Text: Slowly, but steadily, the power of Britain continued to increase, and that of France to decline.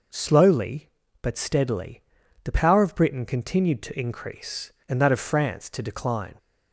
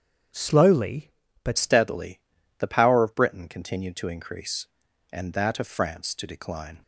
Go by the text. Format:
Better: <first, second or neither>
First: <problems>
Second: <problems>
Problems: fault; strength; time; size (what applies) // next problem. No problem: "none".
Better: first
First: none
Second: starts louder than the rest; strong; until 1.6 s; 7.5 dB // changes voice at "steadily"; from 1.5 s on; 5.3 s long